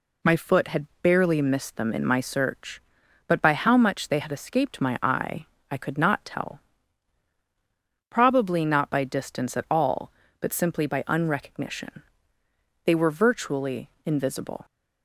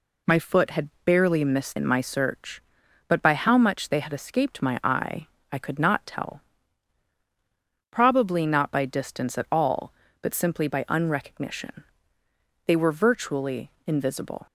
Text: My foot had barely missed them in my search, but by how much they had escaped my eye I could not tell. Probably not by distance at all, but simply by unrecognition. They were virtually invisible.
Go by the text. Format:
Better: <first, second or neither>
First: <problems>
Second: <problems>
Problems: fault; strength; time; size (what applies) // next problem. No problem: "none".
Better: first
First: pauses between "eye" and "I"; slight; at 5.4 s; 0.24 s long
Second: skips "them"; at 1.7 s // pauses between "eye" and "I"; slight; at 5.2 s; 0.24 s long